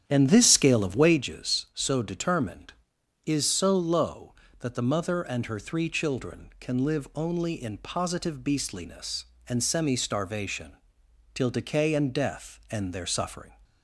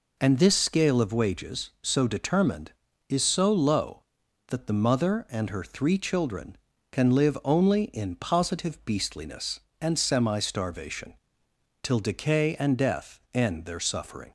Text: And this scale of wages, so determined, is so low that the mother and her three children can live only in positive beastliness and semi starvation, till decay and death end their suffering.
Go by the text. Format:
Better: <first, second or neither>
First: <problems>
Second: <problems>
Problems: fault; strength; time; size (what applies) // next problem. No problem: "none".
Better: second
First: starts louder than the rest; strong; until 1.2 s; 9.5 dB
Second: none